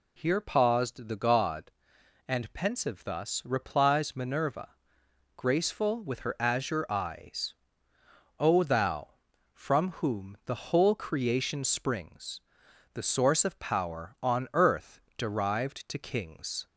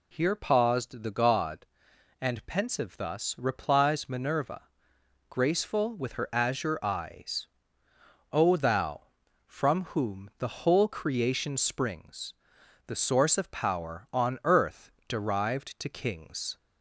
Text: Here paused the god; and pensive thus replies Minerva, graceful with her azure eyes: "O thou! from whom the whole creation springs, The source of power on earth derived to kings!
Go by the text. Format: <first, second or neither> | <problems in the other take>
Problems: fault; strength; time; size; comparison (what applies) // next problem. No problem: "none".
neither | pauses between "earth" and "derived"; slight; the same in both